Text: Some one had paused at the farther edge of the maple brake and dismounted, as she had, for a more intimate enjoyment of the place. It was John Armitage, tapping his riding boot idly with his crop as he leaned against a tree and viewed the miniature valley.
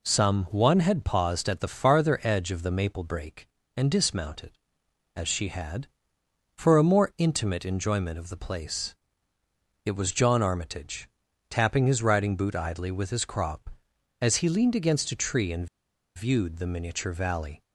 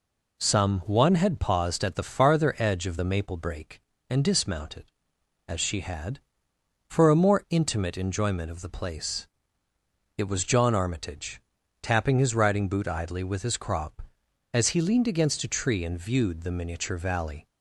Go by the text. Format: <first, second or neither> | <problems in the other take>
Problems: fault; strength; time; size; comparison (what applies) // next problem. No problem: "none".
second | pauses between "and" and "viewed"; noticeable; at 15.6 s; 0.49 s long